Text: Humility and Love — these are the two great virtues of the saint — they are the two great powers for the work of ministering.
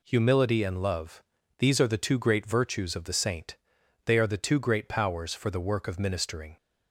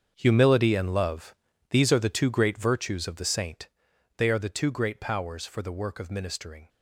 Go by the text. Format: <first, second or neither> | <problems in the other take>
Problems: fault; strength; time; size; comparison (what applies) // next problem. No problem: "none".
first | gets quieter; strong; throughout; 13.5 dB